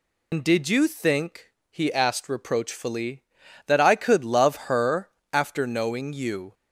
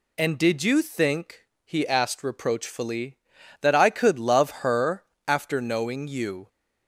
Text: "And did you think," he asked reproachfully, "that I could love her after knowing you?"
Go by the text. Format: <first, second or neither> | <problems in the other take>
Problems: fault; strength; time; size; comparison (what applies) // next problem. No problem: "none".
second | loses the start of "And"; at 0.3 s; 85 ms // pauses between "her" and "after"; slight; at 5.1 s; 0.20 s long; slight in the second